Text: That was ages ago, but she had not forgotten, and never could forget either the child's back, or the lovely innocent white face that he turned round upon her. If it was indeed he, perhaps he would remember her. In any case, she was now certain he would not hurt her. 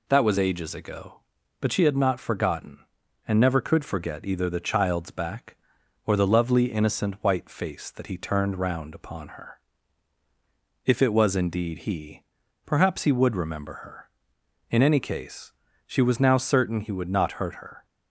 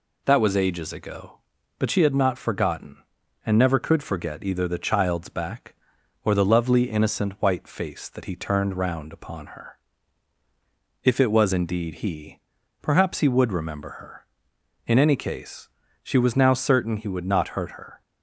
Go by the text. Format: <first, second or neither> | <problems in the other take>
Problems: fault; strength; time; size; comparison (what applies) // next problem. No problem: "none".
neither | none